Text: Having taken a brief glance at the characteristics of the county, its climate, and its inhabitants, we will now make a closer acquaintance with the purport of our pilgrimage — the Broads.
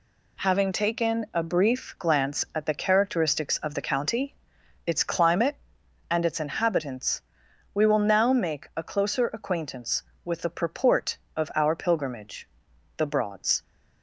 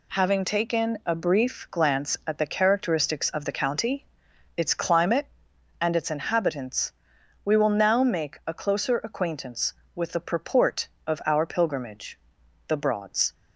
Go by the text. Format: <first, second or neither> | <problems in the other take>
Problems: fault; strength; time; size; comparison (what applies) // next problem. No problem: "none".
neither | none